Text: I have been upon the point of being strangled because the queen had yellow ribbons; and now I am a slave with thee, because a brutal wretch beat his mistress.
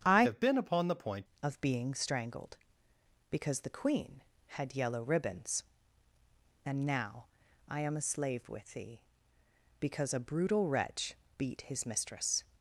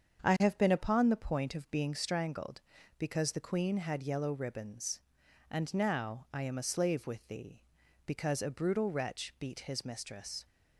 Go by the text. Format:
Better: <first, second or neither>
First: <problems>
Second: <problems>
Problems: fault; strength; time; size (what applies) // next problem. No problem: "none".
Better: second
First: starts louder than the rest; strong; until 1.0 s; 8.5 dB // changes voice from "have" to "point"; from 0.2 to 1.2 s; 1.0 s long // pauses between "now" and "I"; at 7.2 s; 0.42 s long // pauses between "wretch" and "beat"; slight; at 11.1 s; 0.24 s long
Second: starts louder than the rest; strong; until 1.2 s; 7.5 dB